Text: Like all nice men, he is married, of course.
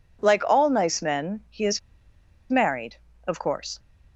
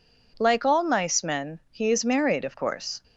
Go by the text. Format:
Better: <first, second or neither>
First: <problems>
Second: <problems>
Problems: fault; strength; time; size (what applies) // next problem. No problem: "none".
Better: second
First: pauses between "is" and "married"; noticeable; at 1.7 s; 0.71 s long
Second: none